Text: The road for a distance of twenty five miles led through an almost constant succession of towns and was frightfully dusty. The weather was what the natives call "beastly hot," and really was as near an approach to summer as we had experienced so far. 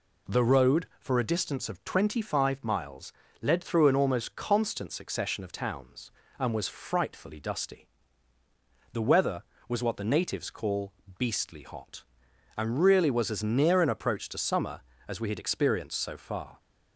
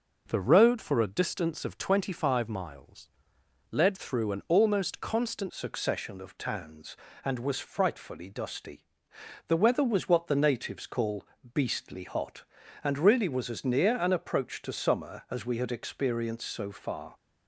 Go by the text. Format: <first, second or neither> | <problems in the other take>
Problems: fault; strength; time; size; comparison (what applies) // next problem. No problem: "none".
first | pauses between "miles" and "led"; noticeable; at 3.0 s; 0.62 s long; slight in the first // changes voice at "succession"; from 5.4 s on; 11.7 s long // pauses between "call" and "beastly"; slight; at 11.2 s; 0.28 s long; slight in the first